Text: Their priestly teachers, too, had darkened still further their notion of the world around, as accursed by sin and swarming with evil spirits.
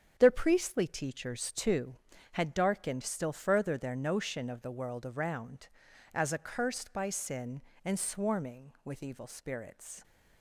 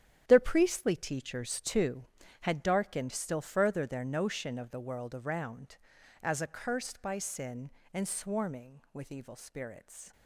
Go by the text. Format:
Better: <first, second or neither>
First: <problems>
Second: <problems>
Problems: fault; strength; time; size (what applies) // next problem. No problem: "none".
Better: first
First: starts louder than the rest; strong; until 1.1 s; 8 dB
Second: gets quieter; strong; throughout; 11 dB // starts louder than the rest; strong; until 1.2 s; 9.5 dB